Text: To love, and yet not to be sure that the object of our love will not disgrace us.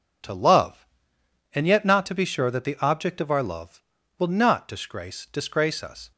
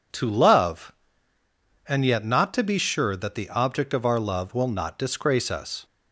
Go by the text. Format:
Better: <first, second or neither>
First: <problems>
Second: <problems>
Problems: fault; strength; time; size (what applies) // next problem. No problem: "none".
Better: second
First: says "disgrace" twice; at 5.2 s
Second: none